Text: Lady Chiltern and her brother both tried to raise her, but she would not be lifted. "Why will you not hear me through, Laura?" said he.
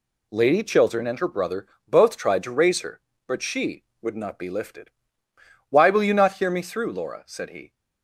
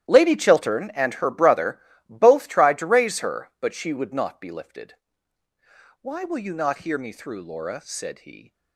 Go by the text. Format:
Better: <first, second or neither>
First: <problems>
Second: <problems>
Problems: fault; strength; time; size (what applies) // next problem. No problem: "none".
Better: first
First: pauses between "brother" and "both"; slight; at 1.6 s; 0.20 s long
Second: gets quieter; strong; throughout; 15 dB // pauses between "brother" and "both"; slight; at 1.7 s; 0.30 s long